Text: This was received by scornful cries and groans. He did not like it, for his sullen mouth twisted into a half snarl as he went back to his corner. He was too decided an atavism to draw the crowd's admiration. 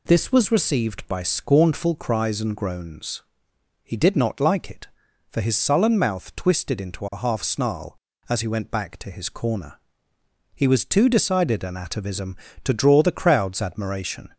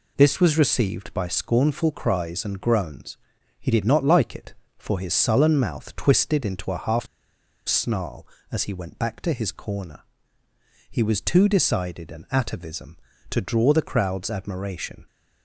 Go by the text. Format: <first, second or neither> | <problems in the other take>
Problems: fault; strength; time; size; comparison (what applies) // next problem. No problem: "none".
first | pauses between "half" and "snarl"; noticeable; at 7.0 s; 0.61 s long